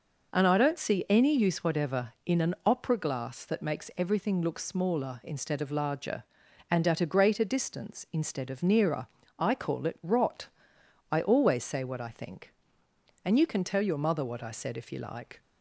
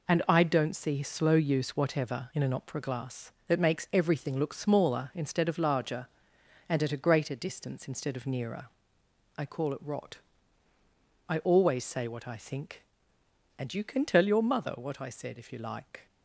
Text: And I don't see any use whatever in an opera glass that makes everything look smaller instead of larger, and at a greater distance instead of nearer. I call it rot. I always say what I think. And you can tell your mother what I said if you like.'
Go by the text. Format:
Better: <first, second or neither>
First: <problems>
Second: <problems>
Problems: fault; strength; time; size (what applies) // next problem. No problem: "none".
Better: first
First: none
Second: says "slow" for "any"; at 1.0 s